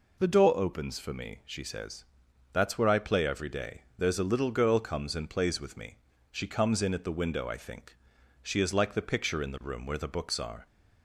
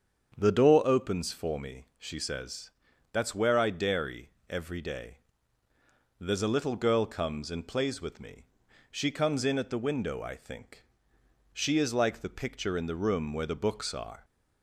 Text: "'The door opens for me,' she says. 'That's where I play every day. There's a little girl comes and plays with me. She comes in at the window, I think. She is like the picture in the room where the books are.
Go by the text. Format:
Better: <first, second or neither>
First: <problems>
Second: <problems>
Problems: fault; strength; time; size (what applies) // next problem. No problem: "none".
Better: first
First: none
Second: starts louder than the rest; strong; until 1.3 s; 7.5 dB // says "dairy" for "play"; at 3.6 s